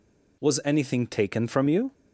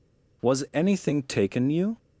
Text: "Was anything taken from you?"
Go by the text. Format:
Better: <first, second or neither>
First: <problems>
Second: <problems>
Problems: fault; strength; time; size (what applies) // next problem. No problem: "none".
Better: first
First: none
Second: skips "from"; at 1.6 s